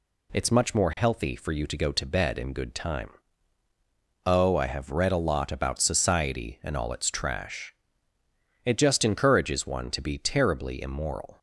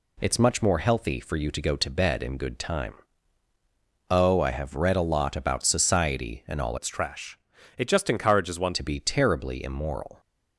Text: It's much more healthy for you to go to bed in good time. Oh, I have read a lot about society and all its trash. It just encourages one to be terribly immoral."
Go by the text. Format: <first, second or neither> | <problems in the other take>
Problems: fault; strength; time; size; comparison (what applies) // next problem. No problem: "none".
first | changes voice from "its" to "one"; from 6.7 to 8.7 s; 2.0 s long